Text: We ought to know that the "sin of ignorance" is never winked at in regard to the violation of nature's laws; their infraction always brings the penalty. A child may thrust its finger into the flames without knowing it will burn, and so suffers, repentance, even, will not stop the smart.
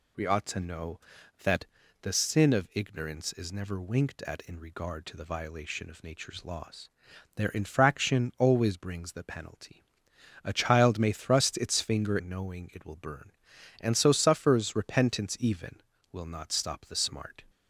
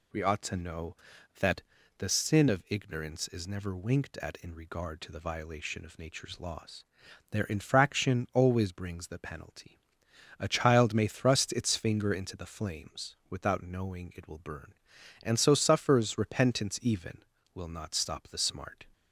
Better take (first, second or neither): second